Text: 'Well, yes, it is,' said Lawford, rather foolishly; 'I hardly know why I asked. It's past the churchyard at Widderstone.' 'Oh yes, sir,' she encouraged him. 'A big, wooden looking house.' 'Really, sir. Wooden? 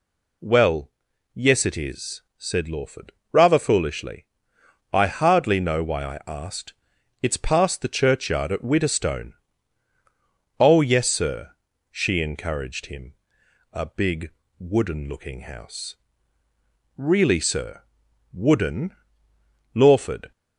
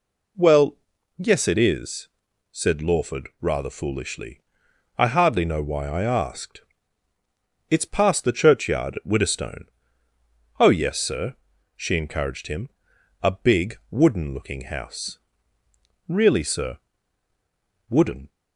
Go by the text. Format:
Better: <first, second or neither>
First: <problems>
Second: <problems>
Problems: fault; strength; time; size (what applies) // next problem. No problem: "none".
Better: second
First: goes on to say "Lawford"; from 19.7 s on; 0.58 s long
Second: none